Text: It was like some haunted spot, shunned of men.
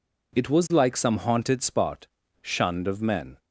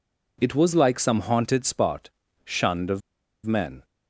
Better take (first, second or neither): first